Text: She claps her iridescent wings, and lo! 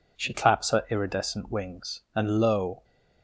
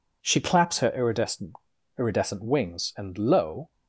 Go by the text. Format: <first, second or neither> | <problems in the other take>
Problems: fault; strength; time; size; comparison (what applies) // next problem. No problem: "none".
first | says "iridescent" twice; at 1.9 s